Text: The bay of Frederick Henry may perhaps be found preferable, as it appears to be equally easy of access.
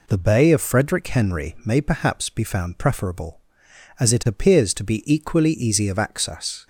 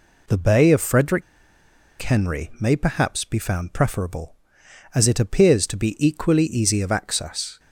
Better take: first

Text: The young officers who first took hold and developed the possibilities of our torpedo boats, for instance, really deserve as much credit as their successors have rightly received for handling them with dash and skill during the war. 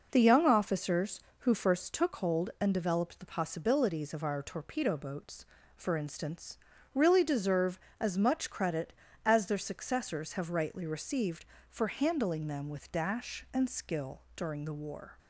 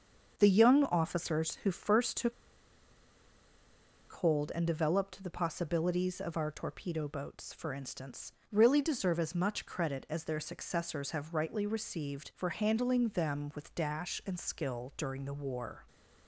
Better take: first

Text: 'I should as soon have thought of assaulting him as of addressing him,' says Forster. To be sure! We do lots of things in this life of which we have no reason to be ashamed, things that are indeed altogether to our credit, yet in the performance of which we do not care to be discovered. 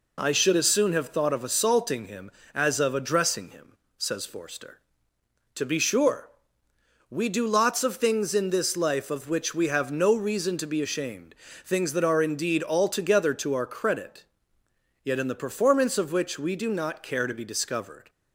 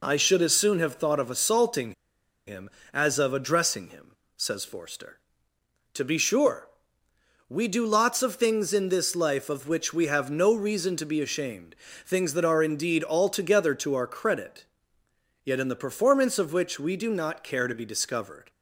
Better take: first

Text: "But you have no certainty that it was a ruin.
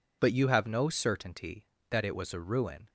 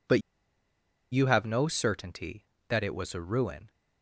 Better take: first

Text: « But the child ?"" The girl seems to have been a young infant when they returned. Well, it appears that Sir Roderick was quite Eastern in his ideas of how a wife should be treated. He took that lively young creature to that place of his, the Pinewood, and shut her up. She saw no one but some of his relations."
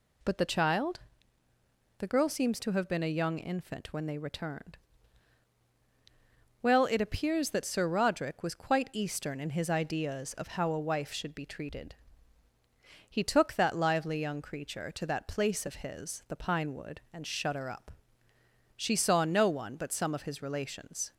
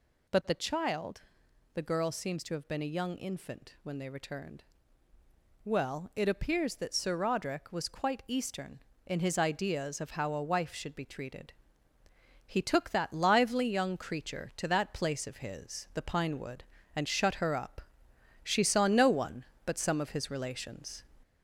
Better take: first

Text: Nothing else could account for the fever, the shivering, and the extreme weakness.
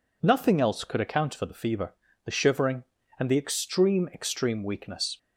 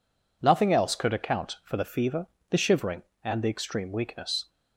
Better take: second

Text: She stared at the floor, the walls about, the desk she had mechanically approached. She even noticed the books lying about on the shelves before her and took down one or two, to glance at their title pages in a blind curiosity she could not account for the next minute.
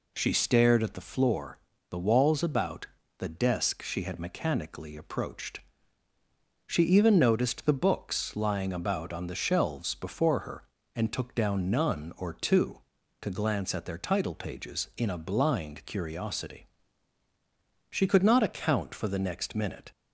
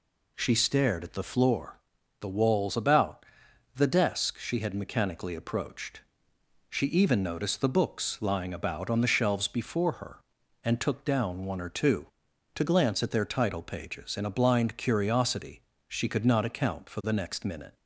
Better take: second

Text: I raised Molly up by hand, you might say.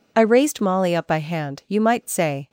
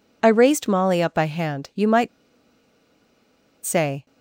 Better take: first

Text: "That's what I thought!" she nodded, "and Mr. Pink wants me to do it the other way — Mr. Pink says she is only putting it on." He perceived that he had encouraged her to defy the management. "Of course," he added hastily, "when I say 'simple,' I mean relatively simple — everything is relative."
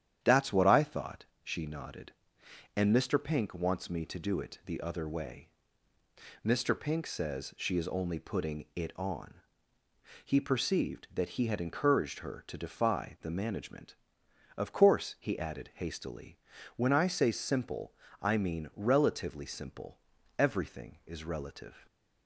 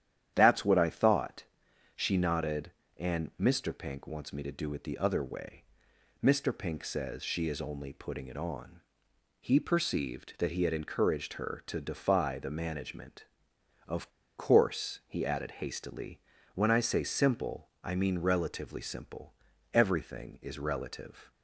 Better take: first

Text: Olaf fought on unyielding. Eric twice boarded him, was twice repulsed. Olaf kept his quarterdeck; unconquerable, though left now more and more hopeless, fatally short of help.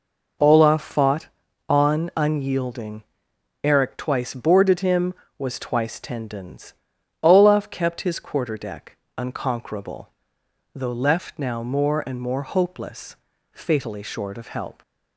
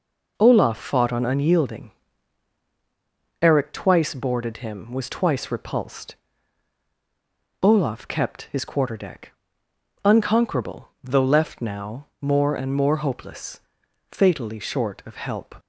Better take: second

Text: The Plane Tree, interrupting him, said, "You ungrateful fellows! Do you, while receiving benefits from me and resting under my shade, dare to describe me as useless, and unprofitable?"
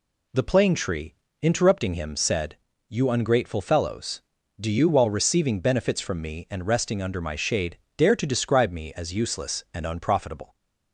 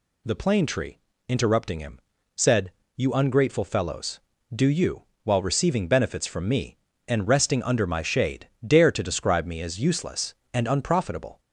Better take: neither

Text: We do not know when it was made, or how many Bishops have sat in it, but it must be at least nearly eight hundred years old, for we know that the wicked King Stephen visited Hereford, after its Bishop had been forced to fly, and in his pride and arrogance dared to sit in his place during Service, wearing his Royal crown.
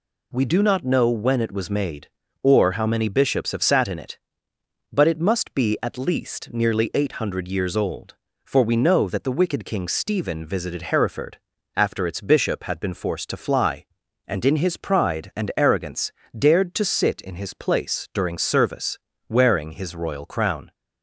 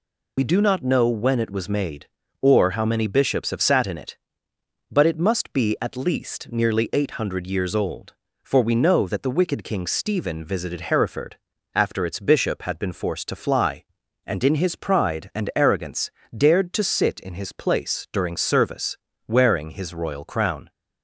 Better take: first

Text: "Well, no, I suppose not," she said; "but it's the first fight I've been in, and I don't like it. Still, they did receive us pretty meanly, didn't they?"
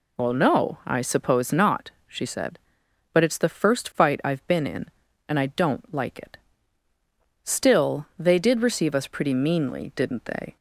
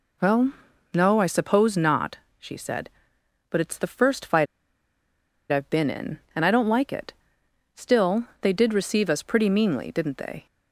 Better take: first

